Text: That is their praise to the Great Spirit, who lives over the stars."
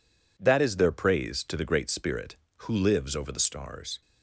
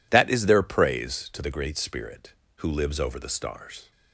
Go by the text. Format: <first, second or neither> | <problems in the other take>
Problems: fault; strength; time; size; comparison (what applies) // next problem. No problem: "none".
neither | none